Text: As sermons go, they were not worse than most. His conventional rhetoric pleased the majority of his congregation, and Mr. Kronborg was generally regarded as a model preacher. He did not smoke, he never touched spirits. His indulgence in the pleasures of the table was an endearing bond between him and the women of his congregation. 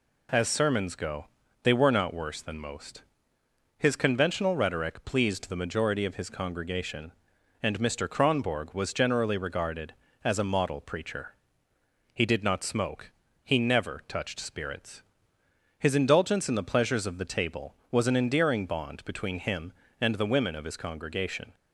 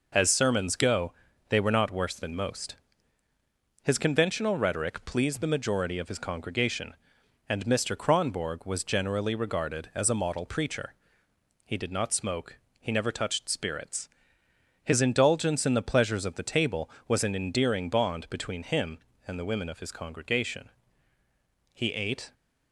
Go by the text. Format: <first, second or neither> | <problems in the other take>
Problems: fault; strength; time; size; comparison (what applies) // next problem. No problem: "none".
first | goes on to say "He ate"; from 21.7 s on; 0.60 s long